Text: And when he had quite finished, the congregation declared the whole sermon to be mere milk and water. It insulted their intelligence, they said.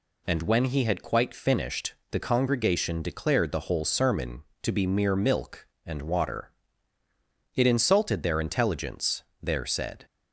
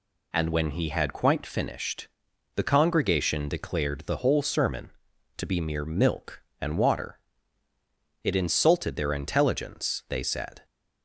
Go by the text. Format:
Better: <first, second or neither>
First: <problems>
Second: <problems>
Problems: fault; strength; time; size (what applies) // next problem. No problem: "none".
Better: second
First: says "there" for "they"; at 9.4 s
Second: none